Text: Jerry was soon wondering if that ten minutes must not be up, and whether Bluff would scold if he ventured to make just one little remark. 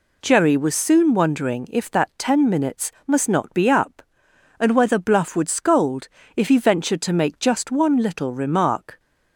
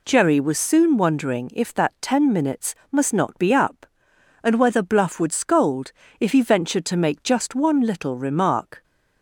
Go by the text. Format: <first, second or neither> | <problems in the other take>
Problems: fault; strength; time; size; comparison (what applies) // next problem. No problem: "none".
neither | pauses between "minutes" and "must"; slight; the same in both // pauses between "scold" and "if"; slight; the same in both